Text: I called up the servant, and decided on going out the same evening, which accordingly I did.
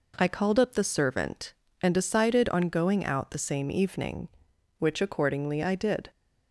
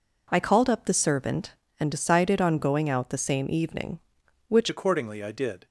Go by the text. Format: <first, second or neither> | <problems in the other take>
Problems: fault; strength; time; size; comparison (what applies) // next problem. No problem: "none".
first | changes voice at "accordingly"; from 4.6 s on; 1.0 s long